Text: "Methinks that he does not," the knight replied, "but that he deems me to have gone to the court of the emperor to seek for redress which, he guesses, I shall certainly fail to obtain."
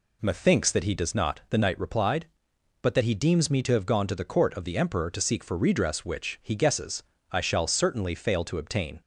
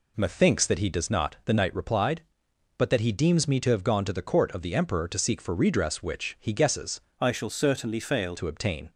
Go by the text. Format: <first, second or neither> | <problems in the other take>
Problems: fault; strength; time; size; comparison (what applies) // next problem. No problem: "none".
first | changes voice from "I" to "fail"; from 7.1 to 8.3 s; 1.2 s long